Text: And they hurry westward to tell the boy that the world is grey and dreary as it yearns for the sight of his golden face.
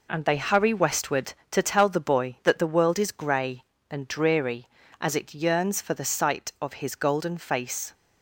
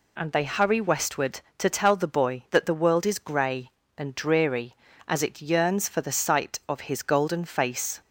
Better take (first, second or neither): second